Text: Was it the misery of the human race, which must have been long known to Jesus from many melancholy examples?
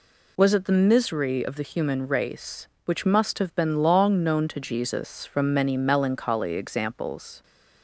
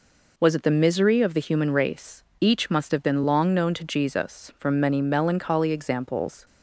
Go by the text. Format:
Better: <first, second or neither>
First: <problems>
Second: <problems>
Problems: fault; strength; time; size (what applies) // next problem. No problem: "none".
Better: first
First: none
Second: says "each" for "which"; at 2.4 s